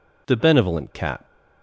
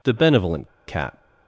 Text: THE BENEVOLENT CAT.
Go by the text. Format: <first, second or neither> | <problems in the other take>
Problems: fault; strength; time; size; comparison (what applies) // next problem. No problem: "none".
first | pauses between "BENEVOLENT" and "CAT"; slight; at 0.6 s; 0.19 s long